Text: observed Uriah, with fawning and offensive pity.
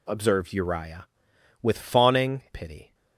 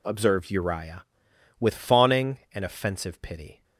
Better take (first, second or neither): second